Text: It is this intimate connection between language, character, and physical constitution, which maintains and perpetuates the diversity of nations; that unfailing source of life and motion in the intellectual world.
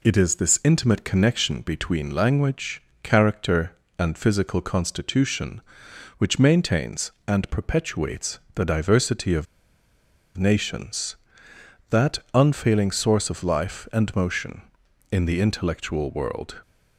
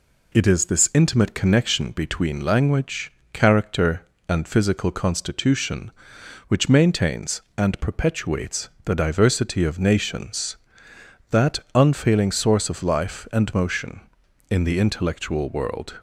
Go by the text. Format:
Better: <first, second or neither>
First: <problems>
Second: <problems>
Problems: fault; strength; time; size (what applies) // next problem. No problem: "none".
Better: second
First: pauses between "perpetuates" and "the"; slight; at 8.3 s; 0.16 s long // pauses between "of" and "nations"; noticeable; at 9.4 s; 0.90 s long // pauses between "that" and "unfailing"; slight; at 12.1 s; 0.16 s long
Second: pauses between "perpetuates" and "the"; slight; at 8.6 s; 0.16 s long // pauses between "that" and "unfailing"; slight; at 11.5 s; 0.16 s long